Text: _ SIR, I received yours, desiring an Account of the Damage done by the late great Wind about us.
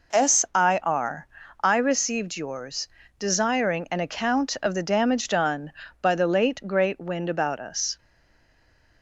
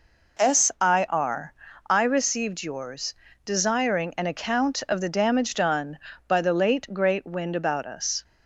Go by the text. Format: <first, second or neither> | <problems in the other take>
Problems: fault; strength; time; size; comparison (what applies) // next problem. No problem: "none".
second | stays silent after the last word; from 7.9 s on; 1.1 s long